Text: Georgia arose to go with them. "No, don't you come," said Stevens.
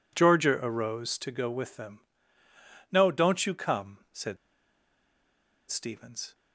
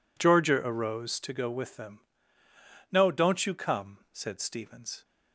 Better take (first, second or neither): second